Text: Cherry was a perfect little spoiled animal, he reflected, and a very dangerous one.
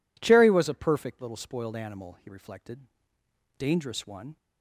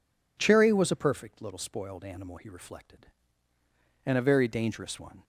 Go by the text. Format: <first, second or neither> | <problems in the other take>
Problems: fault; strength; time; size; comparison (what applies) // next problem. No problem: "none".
second | skips "and a very"; at 3.1 s